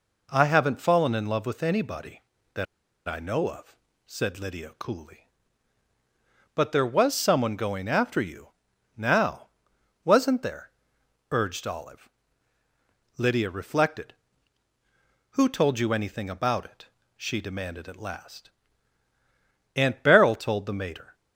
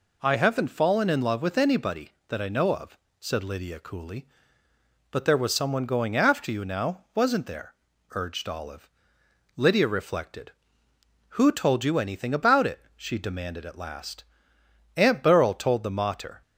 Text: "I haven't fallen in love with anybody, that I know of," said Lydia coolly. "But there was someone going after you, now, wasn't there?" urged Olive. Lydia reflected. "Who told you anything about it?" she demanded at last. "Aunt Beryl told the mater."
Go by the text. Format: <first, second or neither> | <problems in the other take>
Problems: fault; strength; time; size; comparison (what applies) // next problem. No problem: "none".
second | pauses between "that" and "I"; at 2.6 s; 0.43 s long